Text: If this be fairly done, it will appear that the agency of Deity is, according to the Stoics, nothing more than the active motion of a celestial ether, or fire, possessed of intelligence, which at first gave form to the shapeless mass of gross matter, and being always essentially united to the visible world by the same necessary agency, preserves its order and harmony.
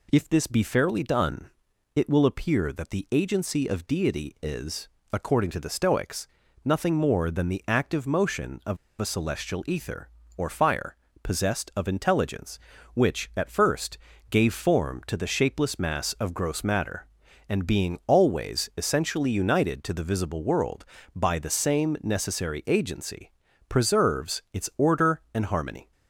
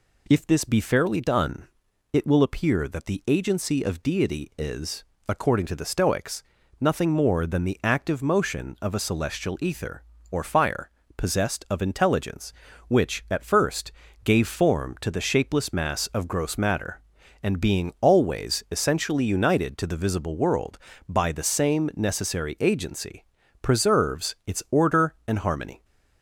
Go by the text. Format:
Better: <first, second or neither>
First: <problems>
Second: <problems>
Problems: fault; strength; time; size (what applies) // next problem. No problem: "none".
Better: second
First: pauses between "of" and "a"; slight; at 8.7 s; 0.24 s long // pauses between "first" and "gave"; slight; at 13.9 s; 0.32 s long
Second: pauses between "first" and "gave"; slight; at 13.9 s; 0.32 s long